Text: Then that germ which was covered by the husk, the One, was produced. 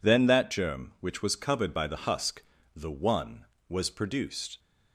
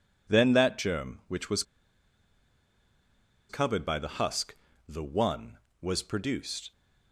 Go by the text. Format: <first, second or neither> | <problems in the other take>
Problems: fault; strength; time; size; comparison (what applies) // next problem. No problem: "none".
first | pauses between "was" and "covered"; strong; at 1.6 s; 1.8 s long